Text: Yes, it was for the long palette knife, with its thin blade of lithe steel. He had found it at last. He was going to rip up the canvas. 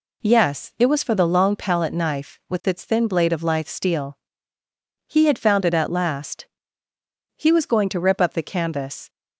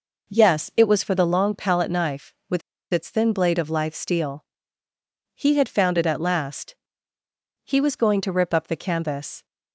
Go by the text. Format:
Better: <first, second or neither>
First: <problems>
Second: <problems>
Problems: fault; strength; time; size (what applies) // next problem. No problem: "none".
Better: first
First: none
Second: pauses between "with" and "its"; slight; at 2.6 s; 0.31 s long